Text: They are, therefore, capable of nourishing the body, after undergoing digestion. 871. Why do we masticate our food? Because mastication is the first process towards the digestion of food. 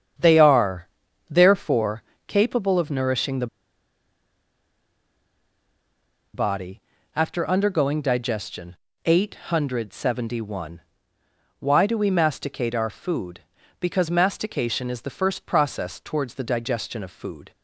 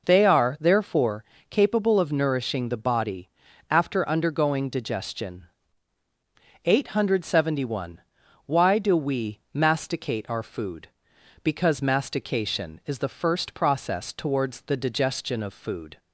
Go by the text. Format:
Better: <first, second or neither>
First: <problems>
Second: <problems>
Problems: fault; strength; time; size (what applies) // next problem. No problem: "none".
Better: second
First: starts louder than the rest; strong; until 1.5 s; 8 dB // pauses between "the" and "body"; strong; at 3.4 s; 2.8 s long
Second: none